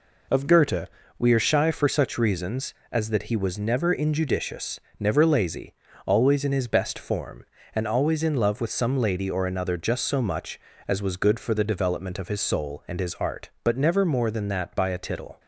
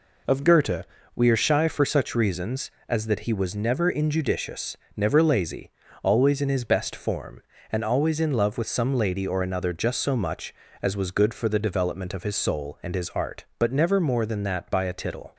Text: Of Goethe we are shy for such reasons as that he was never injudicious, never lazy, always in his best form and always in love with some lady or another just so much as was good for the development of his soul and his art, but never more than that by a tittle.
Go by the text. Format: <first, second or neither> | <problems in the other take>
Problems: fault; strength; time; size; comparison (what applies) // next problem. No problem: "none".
neither | pauses between "Goethe" and "we"; slight; the same in both